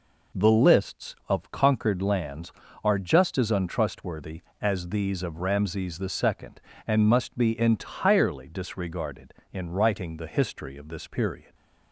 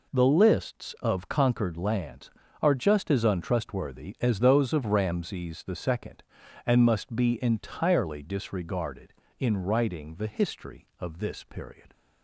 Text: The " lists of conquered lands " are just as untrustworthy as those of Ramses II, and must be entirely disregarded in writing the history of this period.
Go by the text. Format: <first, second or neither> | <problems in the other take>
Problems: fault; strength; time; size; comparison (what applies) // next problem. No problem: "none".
second | says "these" for "those"; at 4.8 s